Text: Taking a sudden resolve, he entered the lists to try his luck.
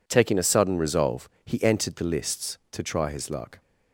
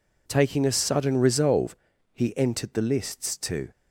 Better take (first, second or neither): first